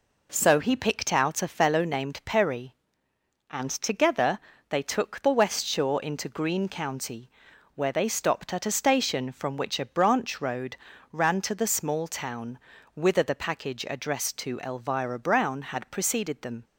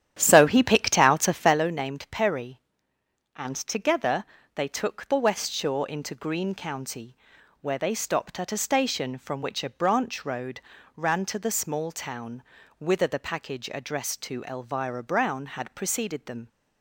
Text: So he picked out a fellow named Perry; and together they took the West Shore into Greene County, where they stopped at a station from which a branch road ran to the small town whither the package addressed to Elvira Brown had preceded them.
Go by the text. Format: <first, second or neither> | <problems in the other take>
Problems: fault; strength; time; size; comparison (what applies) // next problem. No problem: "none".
first | starts louder than the rest; strong; until 1.6 s; 10.5 dB // pauses between "together" and "they"; slight; at 4.2 s; 0.30 s long; slight in the first // pauses between "road" and "ran"; slight; at 10.6 s; 0.36 s long; slight in the first // pauses between "town" and "whither"; slight; at 12.4 s; 0.34 s long; slight in the first